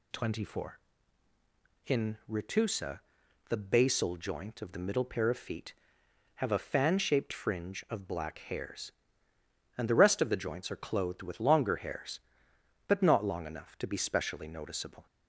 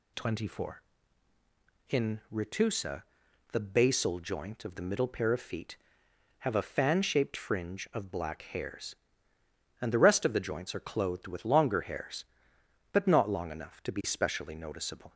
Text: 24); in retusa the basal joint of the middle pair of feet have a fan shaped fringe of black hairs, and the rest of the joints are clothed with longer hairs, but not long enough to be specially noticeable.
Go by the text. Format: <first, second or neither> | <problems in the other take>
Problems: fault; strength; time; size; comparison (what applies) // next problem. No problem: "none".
neither | pauses between "retusa" and "the"; noticeable; the same in both